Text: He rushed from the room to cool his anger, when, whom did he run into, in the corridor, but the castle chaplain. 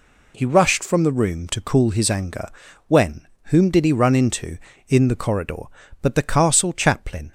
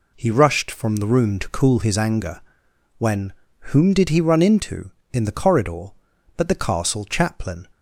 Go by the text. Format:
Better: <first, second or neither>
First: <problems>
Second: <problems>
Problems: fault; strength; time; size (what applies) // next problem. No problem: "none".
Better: neither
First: none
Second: none